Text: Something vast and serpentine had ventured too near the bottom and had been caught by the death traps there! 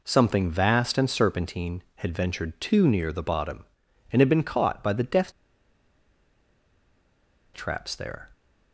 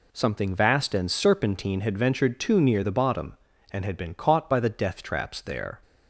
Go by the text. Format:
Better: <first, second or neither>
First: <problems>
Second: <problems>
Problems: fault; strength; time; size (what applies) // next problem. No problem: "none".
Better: second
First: pauses between "death" and "traps"; strong; at 5.3 s; 2.2 s long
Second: none